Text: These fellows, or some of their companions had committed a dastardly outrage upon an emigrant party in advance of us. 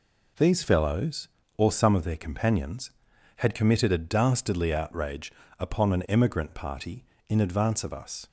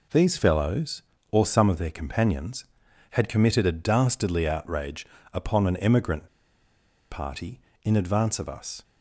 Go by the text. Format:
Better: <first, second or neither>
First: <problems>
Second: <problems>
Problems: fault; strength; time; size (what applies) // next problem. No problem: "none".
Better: first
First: pauses between "outrage" and "upon"; slight; at 5.3 s; 0.28 s long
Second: pauses between "outrage" and "upon"; slight; at 5.0 s; 0.28 s long // pauses between "emigrant" and "party"; noticeable; at 6.2 s; 0.85 s long